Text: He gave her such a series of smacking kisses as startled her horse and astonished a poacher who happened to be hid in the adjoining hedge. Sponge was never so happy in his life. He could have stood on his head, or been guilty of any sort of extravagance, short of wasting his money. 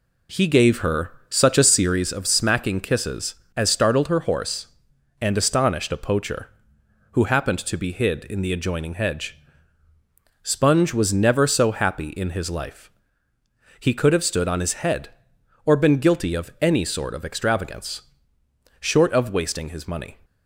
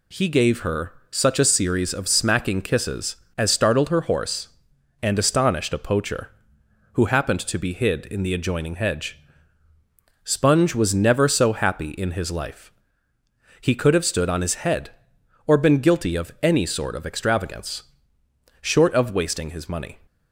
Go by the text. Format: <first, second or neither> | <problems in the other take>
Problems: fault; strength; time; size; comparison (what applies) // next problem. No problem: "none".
second | starts louder than the rest; slight; until 2.1 s; 3 dB // pauses between "her" and "such"; slight; at 1.1 s; 0.18 s long; slight in the second